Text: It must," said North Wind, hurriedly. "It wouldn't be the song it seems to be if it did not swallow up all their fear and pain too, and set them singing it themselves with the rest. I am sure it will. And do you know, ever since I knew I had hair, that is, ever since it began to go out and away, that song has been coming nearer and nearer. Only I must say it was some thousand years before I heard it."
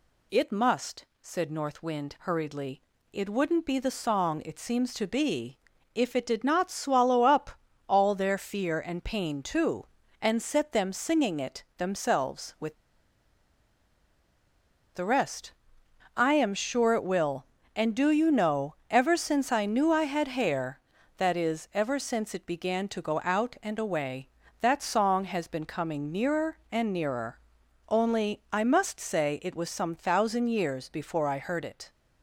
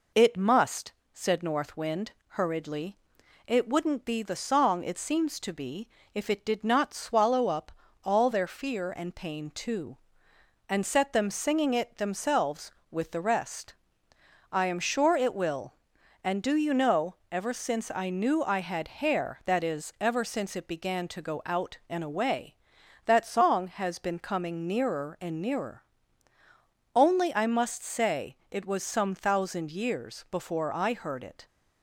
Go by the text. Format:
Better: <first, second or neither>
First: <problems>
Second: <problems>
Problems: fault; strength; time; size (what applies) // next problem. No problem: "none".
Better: second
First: pauses between "be" and "if"; at 5.5 s; 0.38 s long // pauses between "up" and "all"; at 7.4 s; 0.38 s long // pauses between "with" and "the"; strong; at 12.7 s; 2.1 s long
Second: pauses between "be" and "if"; slight; at 5.8 s; 0.24 s long // pauses between "up" and "all"; slight; at 7.7 s; 0.34 s long